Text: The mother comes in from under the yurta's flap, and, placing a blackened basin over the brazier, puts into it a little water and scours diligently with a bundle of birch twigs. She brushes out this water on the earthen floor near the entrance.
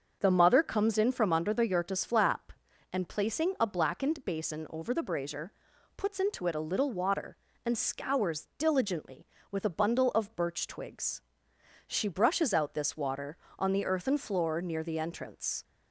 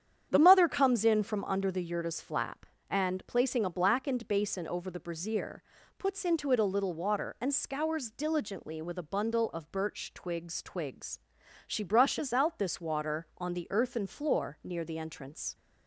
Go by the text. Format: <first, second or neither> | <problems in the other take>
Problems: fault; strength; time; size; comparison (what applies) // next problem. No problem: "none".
first | starts louder than the rest; strong; until 1.3 s; 9 dB; also in the first // says "twigs" twice; at 10.6 s